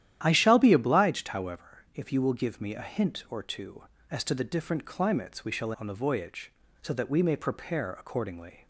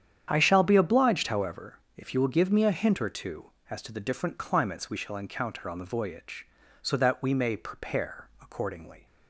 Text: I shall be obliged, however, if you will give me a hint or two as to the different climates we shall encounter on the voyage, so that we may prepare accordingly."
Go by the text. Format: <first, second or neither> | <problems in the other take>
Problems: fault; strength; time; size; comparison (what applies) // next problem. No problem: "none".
second | starts louder than the rest; strong; until 1.2 s; 11.5 dB; strong in the second // skips "encounter"; at 5.7 s